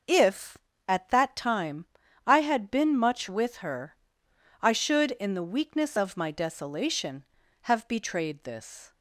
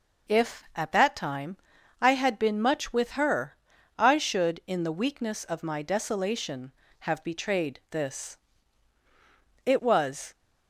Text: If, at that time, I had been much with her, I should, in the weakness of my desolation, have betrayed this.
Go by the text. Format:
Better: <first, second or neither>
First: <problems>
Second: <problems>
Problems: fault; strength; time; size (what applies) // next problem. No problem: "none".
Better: first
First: none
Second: goes on to say "It was"; noticeable; from 9.6 s on; 0.69 s long